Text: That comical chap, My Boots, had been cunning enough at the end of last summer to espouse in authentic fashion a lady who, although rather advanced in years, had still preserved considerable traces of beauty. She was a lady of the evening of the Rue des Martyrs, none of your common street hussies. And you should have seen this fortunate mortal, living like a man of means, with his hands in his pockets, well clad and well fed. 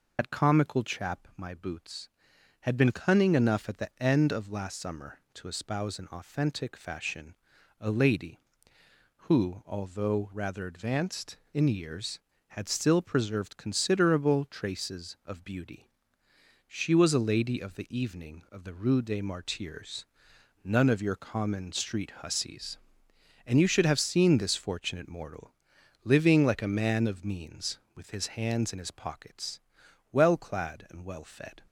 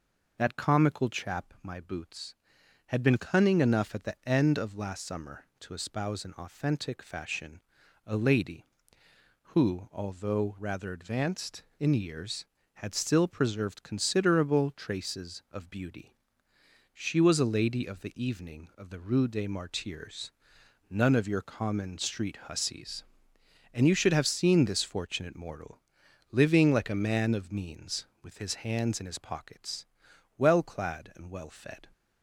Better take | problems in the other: second | loses the start of "That"; at 0.1 s; 55 ms // pauses between "fashion" and "a"; at 7.3 s; 0.44 s long; also in the second

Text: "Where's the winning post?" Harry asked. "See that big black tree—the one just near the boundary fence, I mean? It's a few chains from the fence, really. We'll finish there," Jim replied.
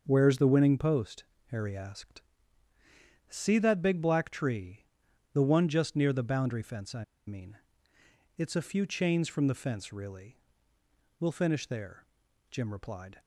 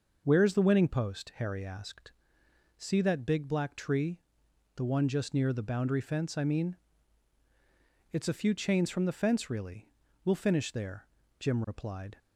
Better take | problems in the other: second | starts louder than the rest; until 1.0 s; 6 dB // pauses between "I" and "mean"; slight; at 7.0 s; 0.23 s long

